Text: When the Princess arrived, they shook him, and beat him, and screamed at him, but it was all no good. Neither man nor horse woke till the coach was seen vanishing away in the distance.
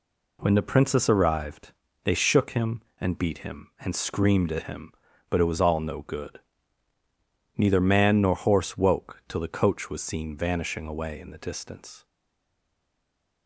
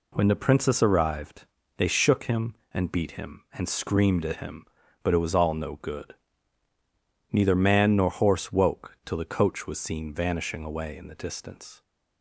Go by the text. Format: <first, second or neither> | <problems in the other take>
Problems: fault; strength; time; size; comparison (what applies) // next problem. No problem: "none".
second | stays silent after the last word; noticeable; from 12.0 s on; 1.4 s long